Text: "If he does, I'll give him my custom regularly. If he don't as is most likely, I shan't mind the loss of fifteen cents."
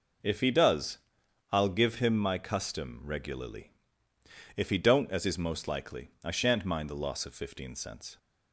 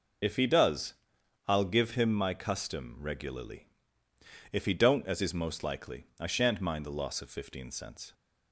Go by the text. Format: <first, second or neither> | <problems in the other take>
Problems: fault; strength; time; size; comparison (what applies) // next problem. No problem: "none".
first | loses the start of "If"; at 0.2 s; 50 ms